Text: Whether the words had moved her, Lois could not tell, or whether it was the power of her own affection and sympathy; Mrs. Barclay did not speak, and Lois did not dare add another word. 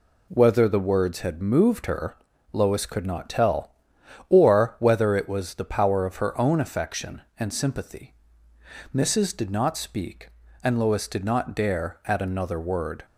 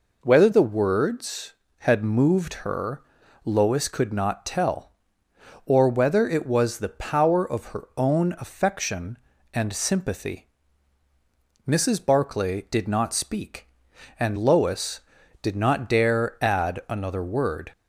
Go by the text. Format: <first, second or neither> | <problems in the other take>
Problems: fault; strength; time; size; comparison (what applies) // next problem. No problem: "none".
second | skips "Barclay"; at 9.3 s